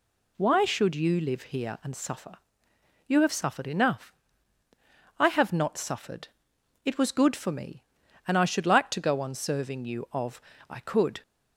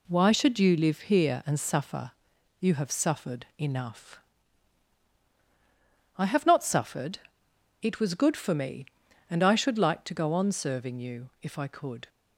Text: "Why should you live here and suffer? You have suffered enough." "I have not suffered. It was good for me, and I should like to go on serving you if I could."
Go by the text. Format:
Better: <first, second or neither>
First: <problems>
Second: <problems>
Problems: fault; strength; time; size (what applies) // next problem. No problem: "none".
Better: second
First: says "of" for "if"; at 10.1 s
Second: none